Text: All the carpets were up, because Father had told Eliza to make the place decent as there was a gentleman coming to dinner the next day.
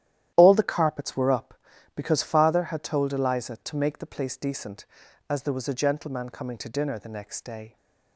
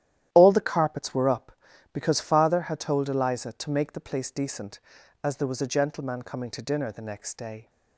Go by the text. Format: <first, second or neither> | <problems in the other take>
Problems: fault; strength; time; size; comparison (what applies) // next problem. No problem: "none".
neither | starts louder than the rest; strong; the same in both